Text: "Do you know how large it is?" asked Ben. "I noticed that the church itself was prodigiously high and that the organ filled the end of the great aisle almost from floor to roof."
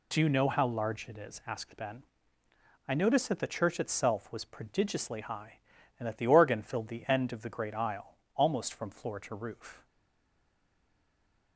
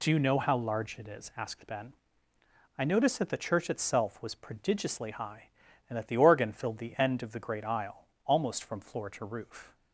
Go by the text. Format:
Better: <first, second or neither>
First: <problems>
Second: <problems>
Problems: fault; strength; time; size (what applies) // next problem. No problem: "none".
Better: second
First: pauses between "aisle" and "almost"; slight; at 8.1 s; 0.16 s long // stays silent after the last word; noticeable; from 9.8 s on; 1.7 s long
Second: pauses between "aisle" and "almost"; slight; at 8.0 s; 0.16 s long